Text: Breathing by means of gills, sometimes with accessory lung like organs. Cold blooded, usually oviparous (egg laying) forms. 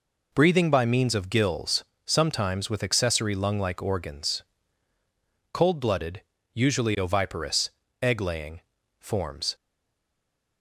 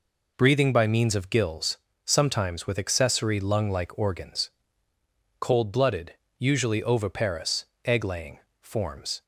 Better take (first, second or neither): second